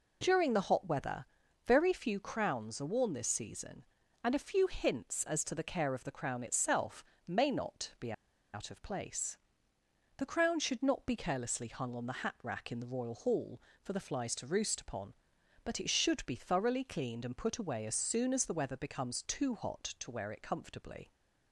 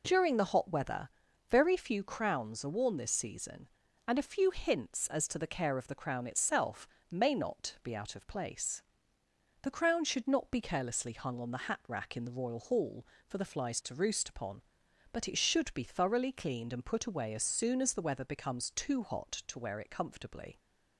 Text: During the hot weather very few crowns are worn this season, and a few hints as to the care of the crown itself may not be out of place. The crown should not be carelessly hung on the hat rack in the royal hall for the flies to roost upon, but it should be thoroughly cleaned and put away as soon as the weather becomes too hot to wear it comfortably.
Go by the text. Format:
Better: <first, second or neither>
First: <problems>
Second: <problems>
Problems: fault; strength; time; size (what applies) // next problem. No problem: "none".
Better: second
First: pauses between "weather" and "very"; at 1.2 s; 0.40 s long // pauses between "itself" and "may"; slight; at 7.0 s; 0.22 s long // pauses between "be" and "out"; at 8.1 s; 0.41 s long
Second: pauses between "weather" and "very"; at 1.0 s; 0.40 s long // pauses between "itself" and "may"; slight; at 6.8 s; 0.22 s long